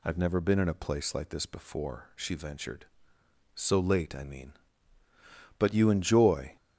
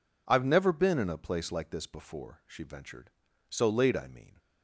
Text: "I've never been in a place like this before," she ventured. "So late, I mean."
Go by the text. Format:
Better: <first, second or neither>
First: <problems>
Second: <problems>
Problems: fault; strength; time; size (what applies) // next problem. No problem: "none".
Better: second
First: goes on to say "But you enjoy"; noticeable; from 5.5 s on; 0.98 s long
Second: none